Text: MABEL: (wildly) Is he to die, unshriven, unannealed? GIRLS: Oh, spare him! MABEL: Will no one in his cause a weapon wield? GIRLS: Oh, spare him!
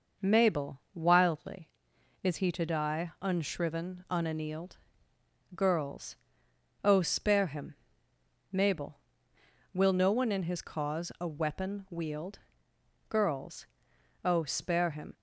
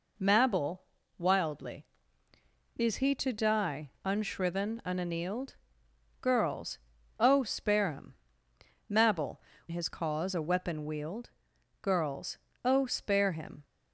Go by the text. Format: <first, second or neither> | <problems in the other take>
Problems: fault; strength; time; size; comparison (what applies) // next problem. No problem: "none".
first | skips "Will no one in"; at 9.5 s